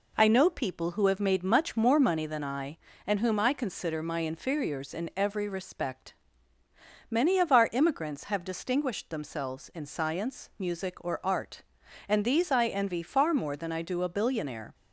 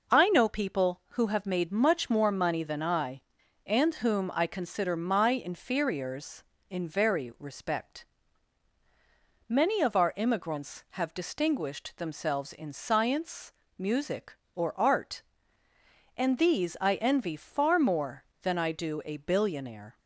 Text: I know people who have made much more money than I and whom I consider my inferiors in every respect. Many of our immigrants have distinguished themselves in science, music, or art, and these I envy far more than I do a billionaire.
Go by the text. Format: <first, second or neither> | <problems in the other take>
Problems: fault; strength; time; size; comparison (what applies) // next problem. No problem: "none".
first | says "very" for "every"; at 6.8 s